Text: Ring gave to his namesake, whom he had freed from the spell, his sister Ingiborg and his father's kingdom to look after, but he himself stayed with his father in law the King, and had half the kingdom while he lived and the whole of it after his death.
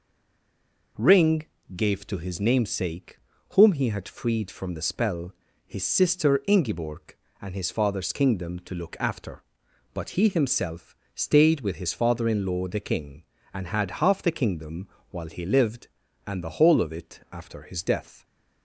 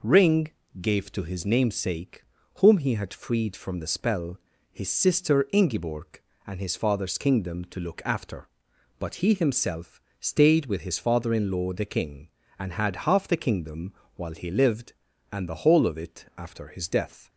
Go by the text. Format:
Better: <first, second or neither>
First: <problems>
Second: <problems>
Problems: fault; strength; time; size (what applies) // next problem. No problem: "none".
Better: second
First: stays silent before the first word; slight; until 0.9 s; 0.9 s long // pauses between "Ring" and "gave"; slight; at 1.4 s; 0.32 s long // pauses between "himself" and "stayed"; slight; at 10.9 s; 0.18 s long // pauses between "kingdom" and "while"; slight; at 14.8 s; 0.24 s long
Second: pauses between "Ring" and "gave"; slight; at 0.4 s; 0.32 s long // pauses between "himself" and "stayed"; slight; at 10.0 s; 0.18 s long // pauses between "kingdom" and "while"; slight; at 13.9 s; 0.24 s long